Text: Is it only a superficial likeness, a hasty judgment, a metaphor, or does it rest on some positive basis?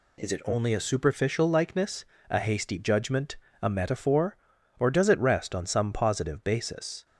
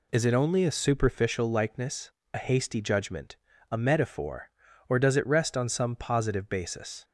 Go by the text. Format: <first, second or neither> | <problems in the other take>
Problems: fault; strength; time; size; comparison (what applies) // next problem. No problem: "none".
neither | none